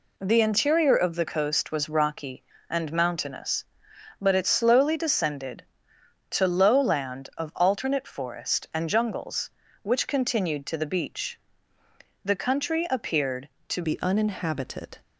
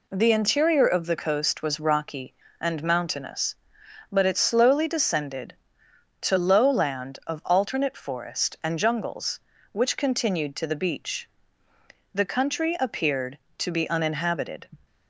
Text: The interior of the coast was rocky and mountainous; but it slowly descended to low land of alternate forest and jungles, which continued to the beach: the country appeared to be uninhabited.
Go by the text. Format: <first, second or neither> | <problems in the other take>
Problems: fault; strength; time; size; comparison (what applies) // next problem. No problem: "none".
second | changes voice at "be"; from 13.8 s on; 1.1 s long